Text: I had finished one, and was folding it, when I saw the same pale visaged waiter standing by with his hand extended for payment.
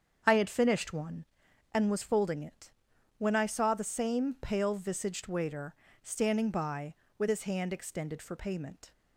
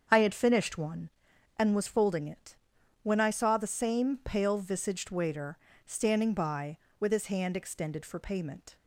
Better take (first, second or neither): neither